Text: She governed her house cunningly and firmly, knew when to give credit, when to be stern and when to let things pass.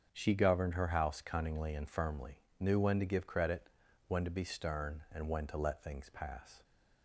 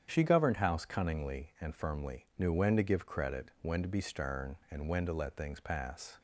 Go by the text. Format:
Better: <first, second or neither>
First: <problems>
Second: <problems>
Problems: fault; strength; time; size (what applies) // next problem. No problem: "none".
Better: first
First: starts louder than the rest; until 1.1 s; 7 dB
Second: starts louder than the rest; strong; until 1.1 s; 8.5 dB // skips "her"; at 0.5 s